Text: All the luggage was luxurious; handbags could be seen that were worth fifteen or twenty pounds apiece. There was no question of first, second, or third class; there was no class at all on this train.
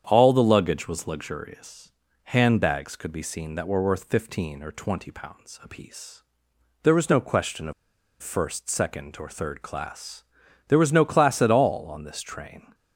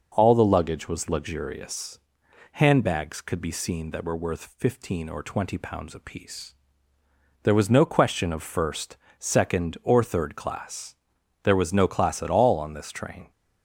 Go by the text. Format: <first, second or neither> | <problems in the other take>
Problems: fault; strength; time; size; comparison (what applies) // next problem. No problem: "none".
second | starts louder than the rest; strong; until 1.0 s; 8 dB // pauses between "of" and "first"; noticeable; at 7.7 s; 0.48 s long